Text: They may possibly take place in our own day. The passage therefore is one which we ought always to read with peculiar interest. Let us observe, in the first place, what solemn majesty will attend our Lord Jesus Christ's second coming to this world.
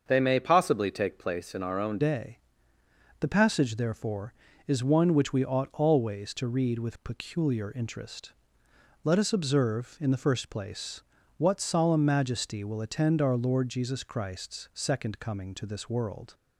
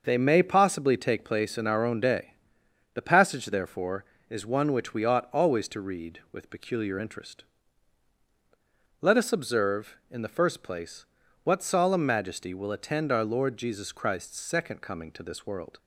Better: second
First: starts louder than the rest; until 1.0 s; 7 dB // changes voice at "day"; from 1.9 s on; 14.4 s long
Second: starts louder than the rest; noticeable; until 1.0 s; 6 dB

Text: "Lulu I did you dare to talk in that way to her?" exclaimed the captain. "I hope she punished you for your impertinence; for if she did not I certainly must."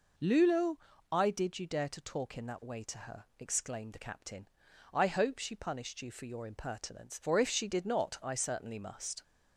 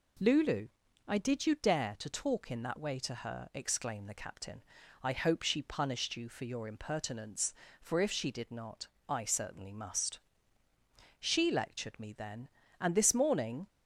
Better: first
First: pauses between "Lulu" and "I"; slight; at 0.7 s; 0.36 s long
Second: pauses between "Lulu" and "I"; slight; at 0.6 s; 0.36 s long // pauses between "not" and "I"; slight; at 8.8 s; 0.22 s long // goes on to say "She lectured me then and this morning"; strong; from 11.1 s on; 2.4 s long

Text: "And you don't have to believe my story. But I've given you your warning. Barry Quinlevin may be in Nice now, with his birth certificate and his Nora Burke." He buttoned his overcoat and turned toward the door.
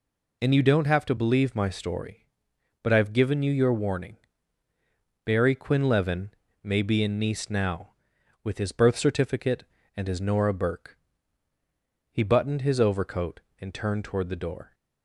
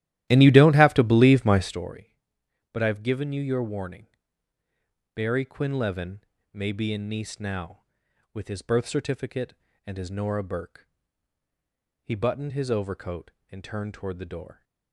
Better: first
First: pauses between "Quinlevin" and "may"; slight; at 6.2 s; 0.32 s long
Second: starts louder than the rest; strong; until 1.8 s; 14 dB // pauses between "Quinlevin" and "may"; slight; at 6.1 s; 0.32 s long

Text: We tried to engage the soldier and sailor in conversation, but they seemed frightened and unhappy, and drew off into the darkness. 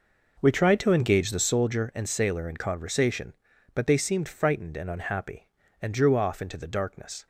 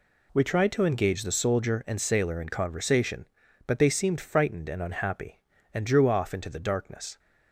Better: second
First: starts louder than the rest; noticeable; until 1.7 s; 5.5 dB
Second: none

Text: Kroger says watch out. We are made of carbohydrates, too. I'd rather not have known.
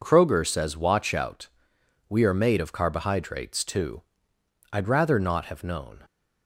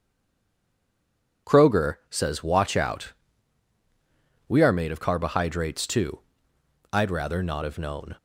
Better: first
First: none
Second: stays silent before the first word; noticeable; until 1.4 s; 1.4 s long

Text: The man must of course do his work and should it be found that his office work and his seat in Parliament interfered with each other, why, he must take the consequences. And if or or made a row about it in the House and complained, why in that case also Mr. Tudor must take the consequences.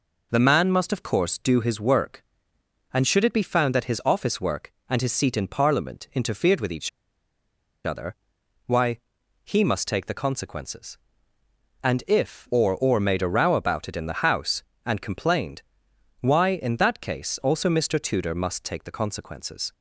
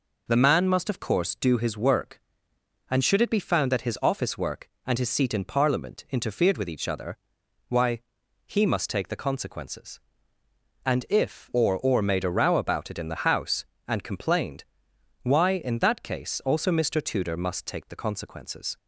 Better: second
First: pauses between "each" and "other"; noticeable; at 6.8 s; 0.95 s long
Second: none

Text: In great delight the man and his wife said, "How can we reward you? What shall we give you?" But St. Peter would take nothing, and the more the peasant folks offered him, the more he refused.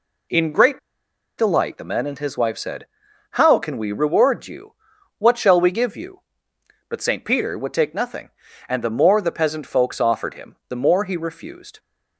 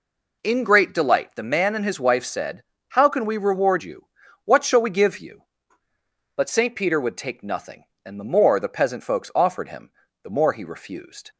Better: second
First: pauses between "great" and "delight"; noticeable; at 0.7 s; 0.59 s long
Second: none

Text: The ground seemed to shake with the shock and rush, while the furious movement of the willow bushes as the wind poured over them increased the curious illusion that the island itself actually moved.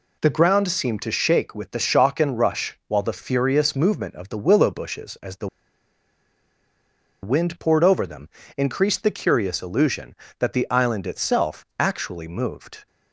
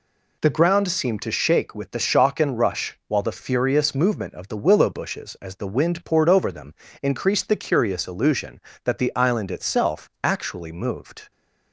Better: second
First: pauses between "the" and "wind"; strong; at 5.4 s; 1.7 s long // pauses between "them" and "increased"; slight; at 8.3 s; 0.26 s long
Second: pauses between "them" and "increased"; slight; at 6.7 s; 0.26 s long

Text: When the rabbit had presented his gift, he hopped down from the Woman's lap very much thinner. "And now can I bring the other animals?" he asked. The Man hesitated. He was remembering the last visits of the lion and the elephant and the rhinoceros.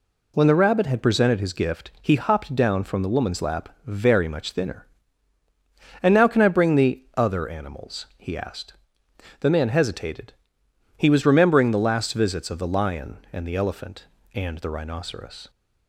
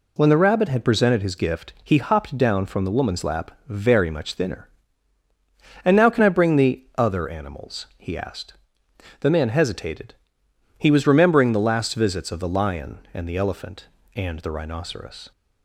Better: neither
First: pauses between "lap" and "very"; slight; at 3.6 s; 0.18 s long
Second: pauses between "lap" and "very"; slight; at 3.5 s; 0.18 s long

